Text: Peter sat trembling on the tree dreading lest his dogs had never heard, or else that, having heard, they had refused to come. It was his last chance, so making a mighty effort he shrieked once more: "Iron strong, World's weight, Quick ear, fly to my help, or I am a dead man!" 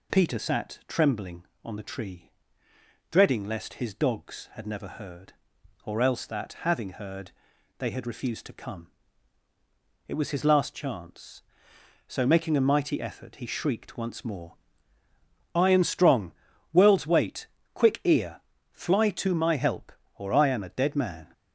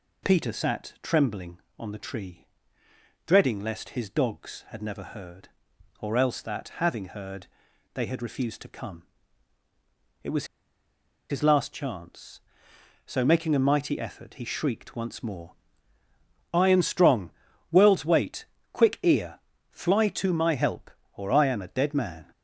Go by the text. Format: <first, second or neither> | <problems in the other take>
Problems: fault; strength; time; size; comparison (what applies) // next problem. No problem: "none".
first | pauses between "tree" and "dreading"; noticeable; at 2.4 s; 0.86 s long; noticeable in the first // pauses between "was" and "his"; noticeable; at 10.4 s; 0.85 s long